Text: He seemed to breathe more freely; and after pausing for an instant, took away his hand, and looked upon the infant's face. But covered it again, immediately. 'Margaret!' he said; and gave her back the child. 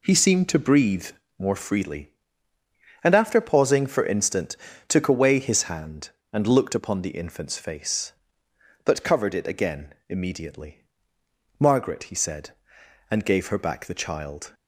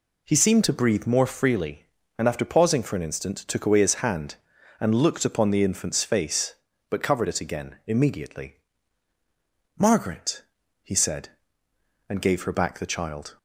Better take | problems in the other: second | pauses between "breathe" and "more"; slight; at 1.1 s; 0.28 s long // skips "an"; at 4.0 s

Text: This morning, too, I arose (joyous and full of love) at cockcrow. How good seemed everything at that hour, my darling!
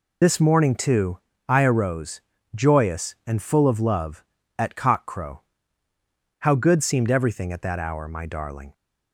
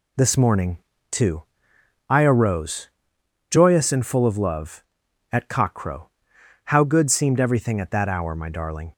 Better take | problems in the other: second | loses the start of "This"; at 0.2 s; 50 ms

